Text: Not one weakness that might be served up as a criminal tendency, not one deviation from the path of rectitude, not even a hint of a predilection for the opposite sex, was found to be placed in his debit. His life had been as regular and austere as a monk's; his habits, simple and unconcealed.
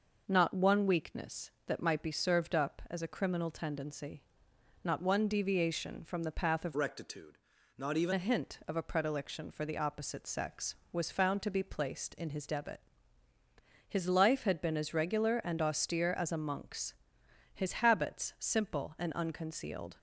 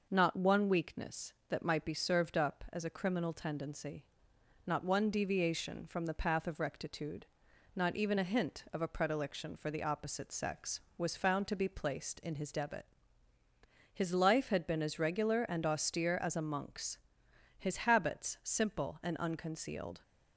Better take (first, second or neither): second